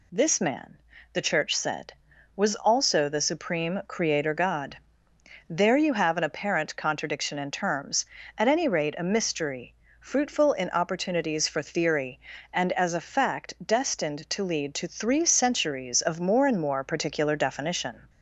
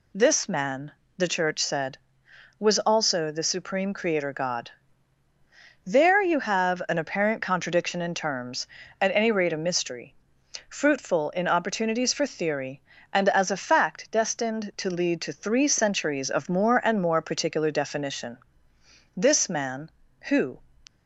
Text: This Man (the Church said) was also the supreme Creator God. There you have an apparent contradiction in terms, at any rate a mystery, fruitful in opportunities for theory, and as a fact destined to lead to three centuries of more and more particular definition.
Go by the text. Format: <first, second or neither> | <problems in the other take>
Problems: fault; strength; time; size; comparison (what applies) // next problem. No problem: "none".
first | goes on to say "This Man Who"; from 19.1 s on; 1.4 s long